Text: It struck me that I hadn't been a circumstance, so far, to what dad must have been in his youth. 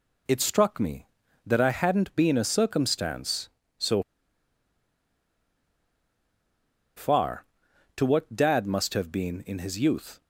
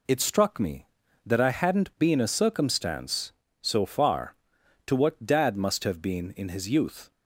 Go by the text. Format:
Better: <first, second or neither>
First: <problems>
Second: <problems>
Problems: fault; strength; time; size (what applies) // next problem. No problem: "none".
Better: second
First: pauses between "so" and "far"; strong; at 4.0 s; 2.9 s long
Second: none